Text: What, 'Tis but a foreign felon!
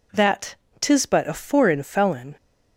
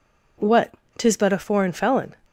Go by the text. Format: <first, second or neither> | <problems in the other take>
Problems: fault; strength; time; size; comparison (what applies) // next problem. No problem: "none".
second | says "That" for "What"; at 0.1 s